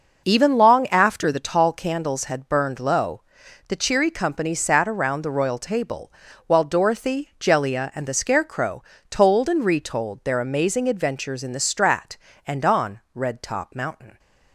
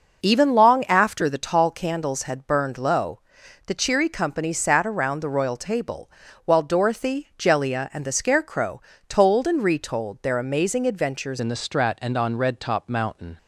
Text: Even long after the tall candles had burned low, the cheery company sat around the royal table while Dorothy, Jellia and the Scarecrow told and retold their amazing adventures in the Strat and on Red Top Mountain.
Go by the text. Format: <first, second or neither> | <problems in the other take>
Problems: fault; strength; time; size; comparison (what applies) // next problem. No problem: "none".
first | pauses between "table" and "while"; slight; at 6.1 s; 0.34 s long; slight in the first // pauses between "Scarecrow" and "told"; slight; at 8.8 s; 0.26 s long; slight in the first // changes voice at "in"; from 11.3 s on; 2.0 s long